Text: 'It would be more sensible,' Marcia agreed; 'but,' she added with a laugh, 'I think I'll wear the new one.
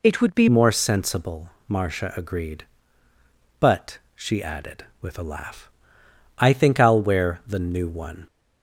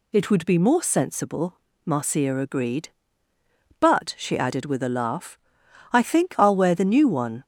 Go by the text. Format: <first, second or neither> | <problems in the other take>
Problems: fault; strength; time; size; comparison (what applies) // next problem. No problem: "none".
second | changes voice at "more"; from 0.4 s on; 7.8 s long